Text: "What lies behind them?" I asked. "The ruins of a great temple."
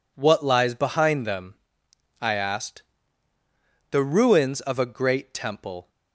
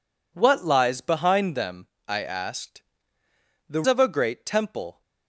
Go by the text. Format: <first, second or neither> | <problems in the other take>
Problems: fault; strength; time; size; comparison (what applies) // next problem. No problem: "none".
first | skips "ruins"; at 3.8 s